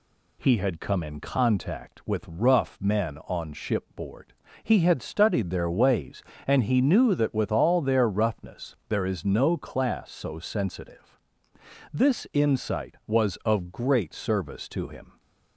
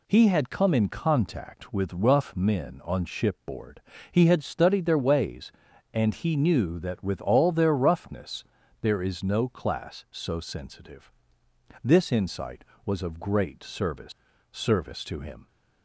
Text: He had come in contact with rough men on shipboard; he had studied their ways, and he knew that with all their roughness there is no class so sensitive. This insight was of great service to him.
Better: first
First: none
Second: pauses between "roughness" and "there"; at 8.4 s; 0.38 s long // says "service" twice; at 14.5 s

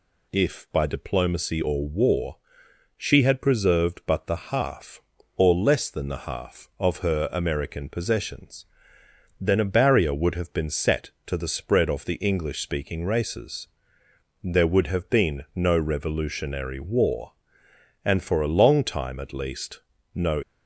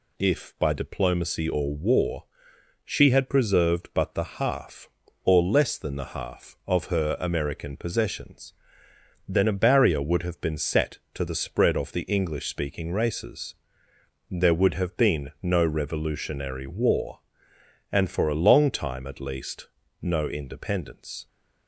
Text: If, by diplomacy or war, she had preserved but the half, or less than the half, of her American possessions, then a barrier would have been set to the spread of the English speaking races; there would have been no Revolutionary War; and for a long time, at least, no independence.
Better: second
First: stops before "independence"; at 20.4 s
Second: none

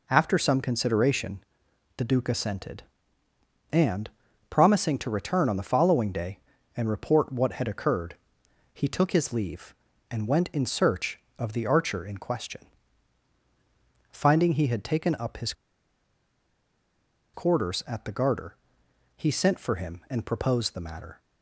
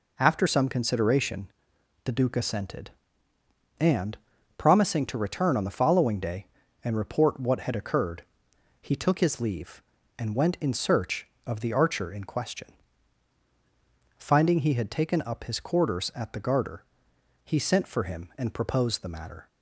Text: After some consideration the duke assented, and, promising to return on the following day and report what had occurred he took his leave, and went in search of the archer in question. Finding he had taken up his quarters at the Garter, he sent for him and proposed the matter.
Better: second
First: pauses between "consideration" and "the"; noticeable; at 1.4 s; 0.54 s long // pauses between "occurred" and "he"; noticeable; at 8.1 s; 0.58 s long // pauses between "his" and "quarters"; strong; at 15.5 s; 1.8 s long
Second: pauses between "consideration" and "the"; noticeable; at 1.5 s; 0.54 s long // pauses between "occurred" and "he"; noticeable; at 8.2 s; 0.58 s long

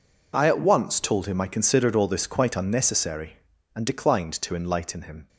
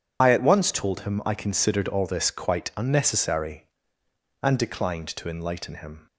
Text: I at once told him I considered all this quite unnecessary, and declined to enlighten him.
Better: first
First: none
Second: loses the start of "I"; at 0.2 s; 40 ms

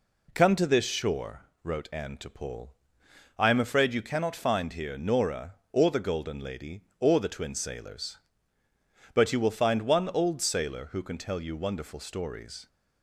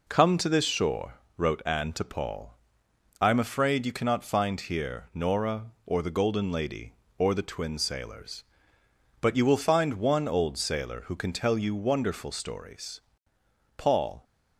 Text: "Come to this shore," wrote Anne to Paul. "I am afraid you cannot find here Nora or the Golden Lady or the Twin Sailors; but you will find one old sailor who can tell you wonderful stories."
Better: first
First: none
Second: goes on to say "Paul"; slight; from 13.7 s on; 0.48 s long

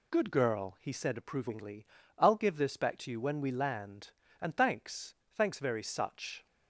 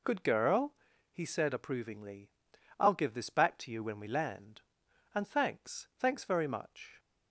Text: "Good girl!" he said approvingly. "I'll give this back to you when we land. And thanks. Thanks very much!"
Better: second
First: says "such" for "much"; at 5.8 s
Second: none

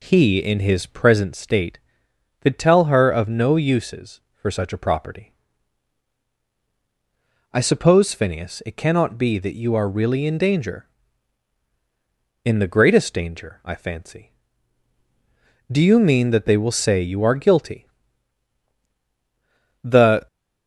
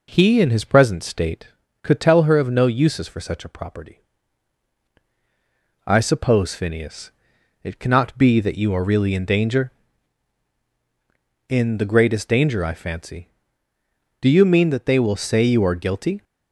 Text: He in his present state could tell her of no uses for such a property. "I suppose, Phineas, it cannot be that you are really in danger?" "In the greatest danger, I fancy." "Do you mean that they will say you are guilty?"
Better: second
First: goes on to say "The"; slight; from 19.8 s on; 0.42 s long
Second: none

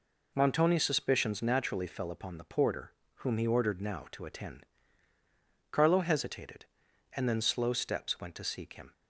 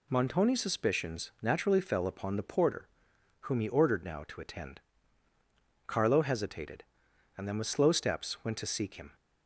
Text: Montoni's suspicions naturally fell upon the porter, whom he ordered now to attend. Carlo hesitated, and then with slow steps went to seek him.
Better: second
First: skips "with"; at 7.4 s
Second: none

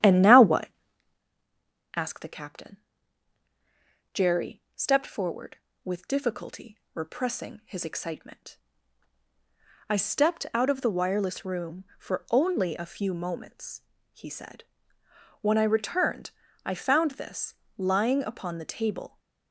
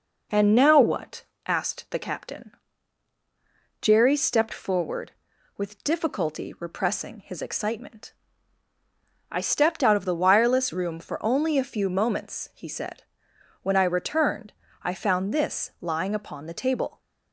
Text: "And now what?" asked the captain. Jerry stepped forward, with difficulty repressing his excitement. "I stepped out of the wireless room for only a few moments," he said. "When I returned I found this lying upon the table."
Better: second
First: starts louder than the rest; strong; until 1.2 s; 10.5 dB // pauses between "difficulty" and "repressing"; slight; at 6.7 s; 0.16 s long // pauses between "returned" and "I"; slight; at 16.3 s; 0.34 s long // pauses between "this" and "lying"; slight; at 17.5 s; 0.24 s long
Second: pauses between "returned" and "I"; slight; at 14.5 s; 0.30 s long

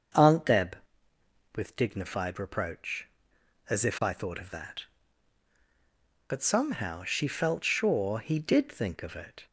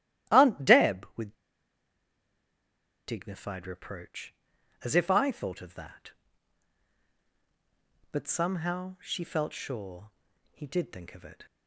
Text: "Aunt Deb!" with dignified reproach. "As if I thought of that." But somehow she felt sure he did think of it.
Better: first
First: starts louder than the rest; until 1.9 s; 6.5 dB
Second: starts louder than the rest; strong; until 1.3 s; 14 dB // pauses between "with" and "dignified"; strong; at 1.3 s; 1.7 s long // pauses between "sure" and "he"; at 10.1 s; 0.42 s long

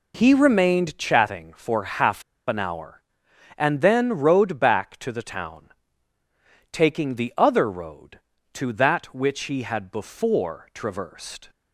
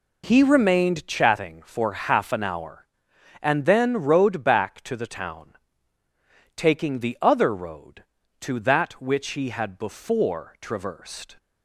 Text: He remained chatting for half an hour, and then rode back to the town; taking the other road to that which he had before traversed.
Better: second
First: pauses between "half" and "an"; slight; at 2.2 s; 0.25 s long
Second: none

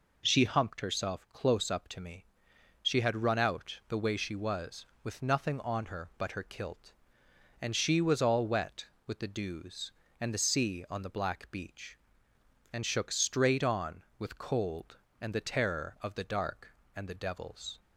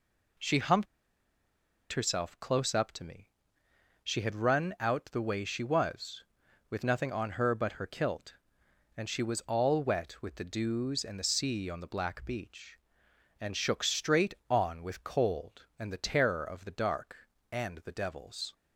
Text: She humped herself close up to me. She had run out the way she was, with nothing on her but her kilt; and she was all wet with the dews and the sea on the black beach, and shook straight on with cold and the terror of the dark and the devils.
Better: first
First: none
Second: pauses between "humped" and "herself"; at 0.8 s; 1.0 s long

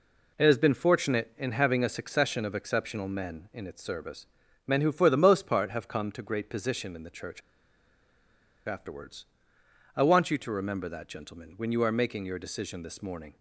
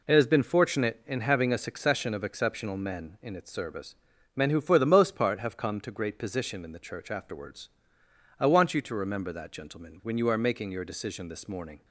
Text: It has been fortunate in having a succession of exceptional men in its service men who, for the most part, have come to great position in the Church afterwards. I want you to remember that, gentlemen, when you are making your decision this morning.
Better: second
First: pauses between "service" and "men"; at 4.2 s; 0.40 s long // pauses between "Church" and "afterwards"; strong; at 7.4 s; 1.2 s long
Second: pauses between "service" and "men"; at 3.9 s; 0.40 s long

